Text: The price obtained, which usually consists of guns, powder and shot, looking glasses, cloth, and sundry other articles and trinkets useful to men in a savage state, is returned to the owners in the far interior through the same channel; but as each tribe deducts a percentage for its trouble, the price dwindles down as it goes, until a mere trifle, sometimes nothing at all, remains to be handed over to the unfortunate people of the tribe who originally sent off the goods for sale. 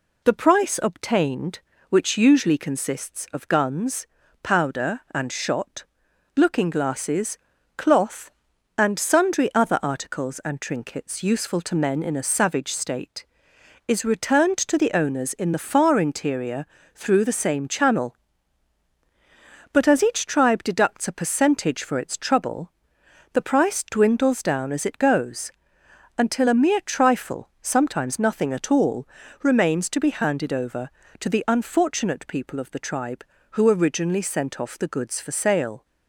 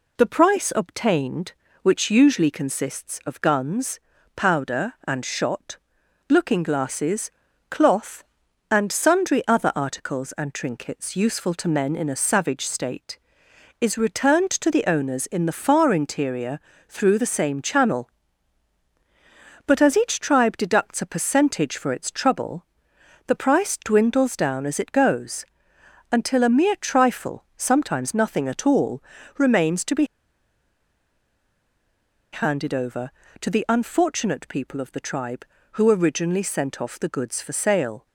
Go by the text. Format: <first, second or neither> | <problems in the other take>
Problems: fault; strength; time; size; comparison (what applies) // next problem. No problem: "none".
first | pauses between "interior" and "through"; slight; at 16.5 s; 0.28 s long; slight in the first // pauses between "be" and "handed"; strong; at 30.0 s; 2.2 s long